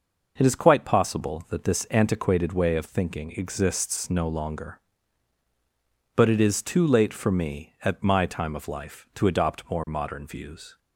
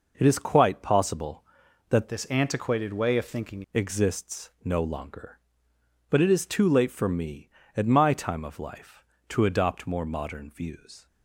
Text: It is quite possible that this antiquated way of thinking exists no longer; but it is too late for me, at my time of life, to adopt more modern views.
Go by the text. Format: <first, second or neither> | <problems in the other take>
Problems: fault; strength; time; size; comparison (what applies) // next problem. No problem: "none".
first | changes voice from "this" to "thinking"; from 2.0 to 3.6 s; 1.6 s long